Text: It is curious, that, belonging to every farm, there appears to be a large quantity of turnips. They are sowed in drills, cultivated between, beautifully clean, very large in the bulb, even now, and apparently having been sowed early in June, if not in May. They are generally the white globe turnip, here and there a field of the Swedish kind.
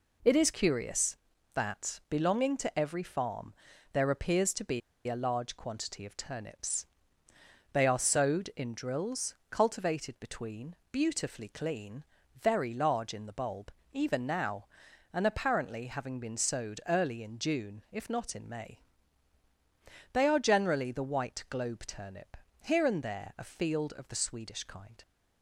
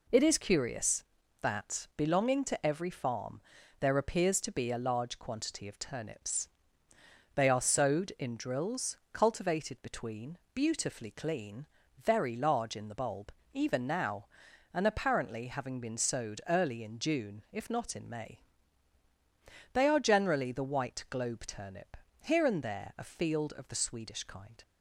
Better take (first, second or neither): second